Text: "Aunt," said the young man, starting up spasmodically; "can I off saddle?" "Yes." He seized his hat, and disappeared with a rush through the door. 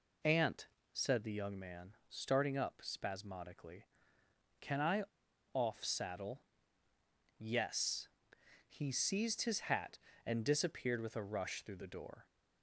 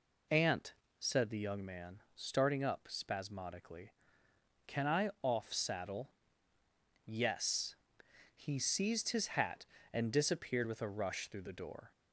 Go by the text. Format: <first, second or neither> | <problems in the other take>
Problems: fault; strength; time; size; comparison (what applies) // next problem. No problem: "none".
second | pauses between "I" and "off"; noticeable; at 5.0 s; 0.51 s long